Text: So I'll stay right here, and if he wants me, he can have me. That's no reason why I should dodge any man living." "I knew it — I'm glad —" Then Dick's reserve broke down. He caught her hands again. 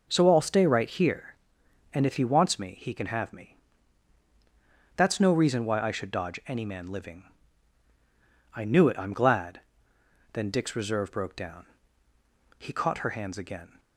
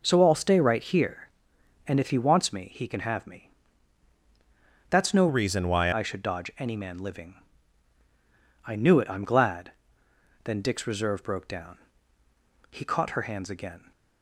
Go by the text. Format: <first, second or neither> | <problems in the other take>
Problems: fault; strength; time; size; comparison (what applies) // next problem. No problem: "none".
first | changes voice from "reason" to "why"; from 5.2 to 5.9 s; 0.7 s long